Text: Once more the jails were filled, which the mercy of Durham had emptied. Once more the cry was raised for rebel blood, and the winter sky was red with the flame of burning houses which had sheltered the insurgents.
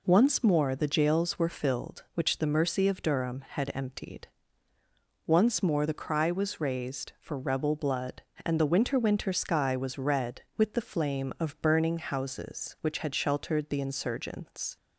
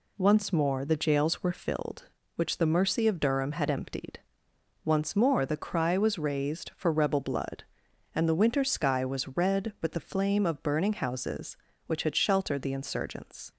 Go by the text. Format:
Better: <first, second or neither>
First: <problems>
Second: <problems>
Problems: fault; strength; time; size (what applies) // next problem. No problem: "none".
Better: second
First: says "winter" twice; at 8.9 s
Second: none